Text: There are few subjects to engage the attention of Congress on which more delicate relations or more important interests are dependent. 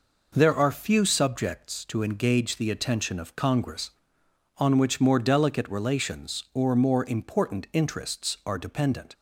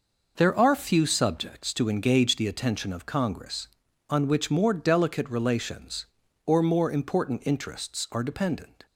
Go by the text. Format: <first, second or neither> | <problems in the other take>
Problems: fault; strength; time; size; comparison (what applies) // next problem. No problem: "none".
neither | none